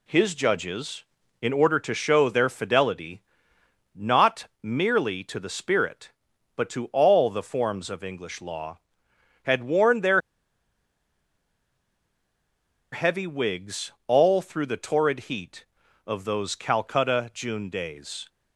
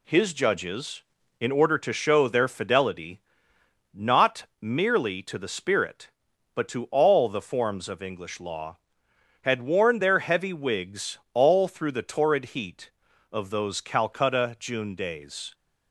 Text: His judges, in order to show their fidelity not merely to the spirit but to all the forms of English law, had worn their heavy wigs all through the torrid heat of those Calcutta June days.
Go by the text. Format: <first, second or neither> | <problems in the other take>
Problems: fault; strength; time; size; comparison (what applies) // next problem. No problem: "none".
second | pauses between "fidelity" and "not"; noticeable; at 3.2 s; 0.72 s long; noticeable in the second // pauses between "not" and "merely"; slight; at 4.4 s; 0.16 s long; slight in the second // pauses between "their" and "heavy"; strong; at 10.2 s; 2.7 s long // pauses between "wigs" and "all"; slight; at 13.9 s; 0.16 s long; slight in the second